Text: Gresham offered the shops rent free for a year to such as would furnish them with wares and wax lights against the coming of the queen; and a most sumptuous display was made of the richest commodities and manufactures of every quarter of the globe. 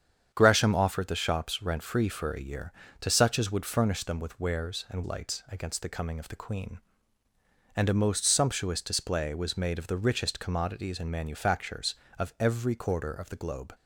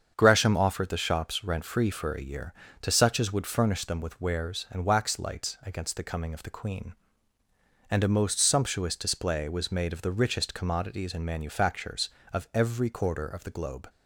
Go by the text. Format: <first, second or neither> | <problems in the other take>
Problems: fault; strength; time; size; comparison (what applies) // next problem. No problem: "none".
second | starts louder than the rest; strong; until 1.3 s; 8 dB; strong in the second // skips "wax"; at 5.0 s